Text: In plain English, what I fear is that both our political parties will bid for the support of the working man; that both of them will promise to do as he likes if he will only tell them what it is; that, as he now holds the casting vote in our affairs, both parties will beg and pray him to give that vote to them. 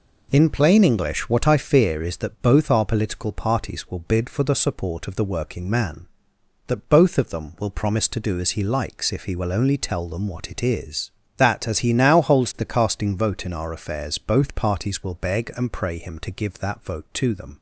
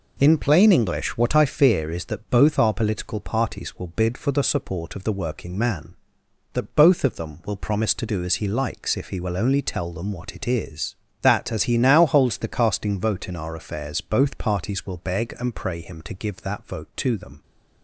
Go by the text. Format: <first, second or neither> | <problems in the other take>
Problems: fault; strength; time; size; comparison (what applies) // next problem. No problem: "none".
neither | none